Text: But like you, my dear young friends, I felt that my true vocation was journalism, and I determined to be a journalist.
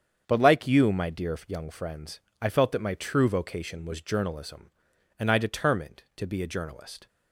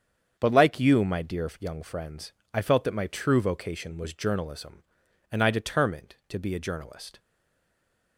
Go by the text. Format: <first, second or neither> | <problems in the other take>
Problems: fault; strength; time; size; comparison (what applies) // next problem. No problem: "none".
first | starts louder than the rest; strong; until 1.3 s; 7.5 dB; strong in the first // stays silent after the last word; from 7.1 s on; 1.0 s long